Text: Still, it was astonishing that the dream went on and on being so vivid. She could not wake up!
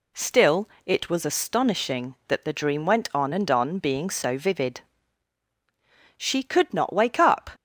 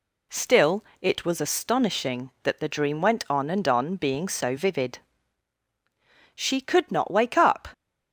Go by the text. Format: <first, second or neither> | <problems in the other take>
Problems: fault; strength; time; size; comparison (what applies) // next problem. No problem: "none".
neither | none